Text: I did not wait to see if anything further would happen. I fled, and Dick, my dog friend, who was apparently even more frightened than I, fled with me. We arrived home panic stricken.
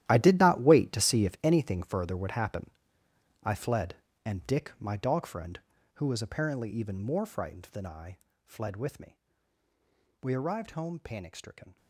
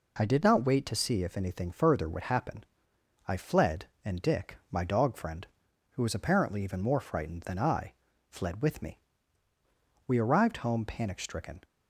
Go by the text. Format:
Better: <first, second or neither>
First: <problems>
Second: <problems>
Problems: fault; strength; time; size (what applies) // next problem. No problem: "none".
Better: second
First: gets quieter; strong; throughout; 16 dB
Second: none